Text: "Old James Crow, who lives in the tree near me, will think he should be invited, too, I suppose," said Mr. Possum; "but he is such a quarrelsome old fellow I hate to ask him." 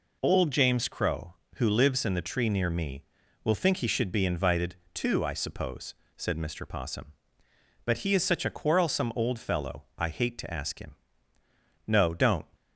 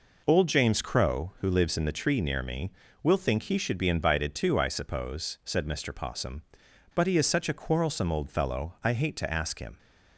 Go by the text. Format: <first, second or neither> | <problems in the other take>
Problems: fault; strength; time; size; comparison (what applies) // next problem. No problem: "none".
second | goes on to say "No don't"; from 11.8 s on; 0.60 s long